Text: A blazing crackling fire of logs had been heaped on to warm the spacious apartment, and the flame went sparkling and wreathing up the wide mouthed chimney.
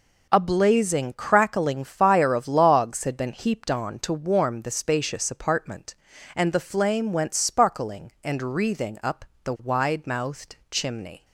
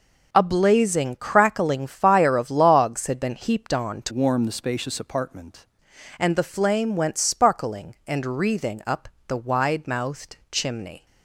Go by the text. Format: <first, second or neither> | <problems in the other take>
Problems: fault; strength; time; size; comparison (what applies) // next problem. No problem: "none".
first | changes voice from "warm" to "apartment"; from 4.1 to 5.6 s; 1.5 s long // pauses between "up" and "the"; slight; at 9.0 s; 0.22 s long; slight in the first // pauses between "mouthed" and "chimney"; slight; at 10.3 s; 0.16 s long; slight in the first